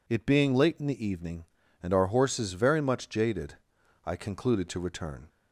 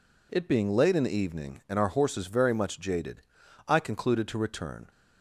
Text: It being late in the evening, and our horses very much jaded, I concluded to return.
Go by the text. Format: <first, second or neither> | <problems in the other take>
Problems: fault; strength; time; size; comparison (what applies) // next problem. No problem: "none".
neither | none